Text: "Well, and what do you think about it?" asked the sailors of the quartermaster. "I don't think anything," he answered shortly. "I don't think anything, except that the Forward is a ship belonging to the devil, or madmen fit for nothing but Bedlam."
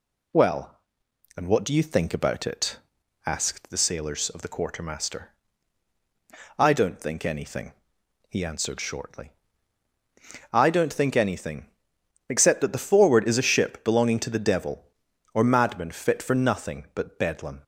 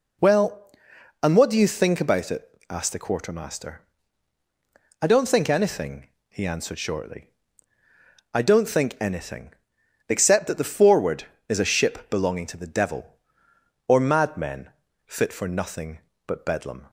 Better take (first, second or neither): first